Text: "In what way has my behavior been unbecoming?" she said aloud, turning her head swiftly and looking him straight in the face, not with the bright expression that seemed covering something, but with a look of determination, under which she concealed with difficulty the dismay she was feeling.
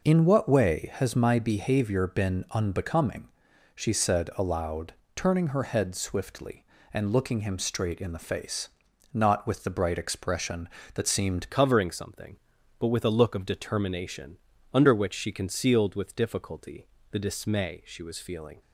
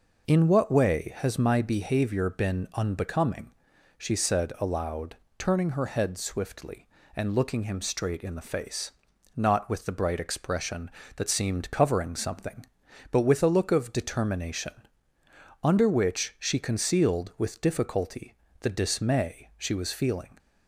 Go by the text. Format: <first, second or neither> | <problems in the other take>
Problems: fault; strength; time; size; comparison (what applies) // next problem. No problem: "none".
second | changes voice at "covering"; from 11.4 s on; 7.2 s long // pauses between "difficulty" and "the"; slight; at 16.8 s; 0.28 s long; slight in the second